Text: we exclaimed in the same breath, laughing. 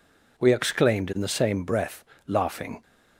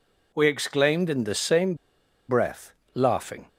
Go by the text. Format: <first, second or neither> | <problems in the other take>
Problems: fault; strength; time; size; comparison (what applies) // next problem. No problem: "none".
first | pauses between "same" and "breath"; noticeable; at 1.7 s; 0.54 s long